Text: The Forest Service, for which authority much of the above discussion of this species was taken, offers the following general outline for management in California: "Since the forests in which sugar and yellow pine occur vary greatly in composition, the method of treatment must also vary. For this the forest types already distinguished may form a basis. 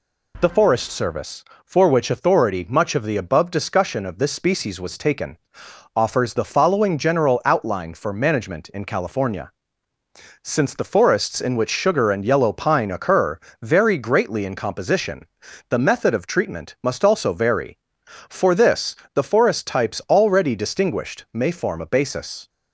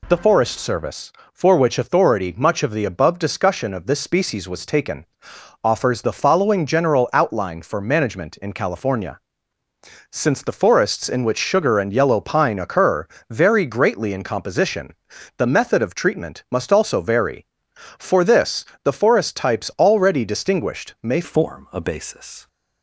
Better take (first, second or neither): first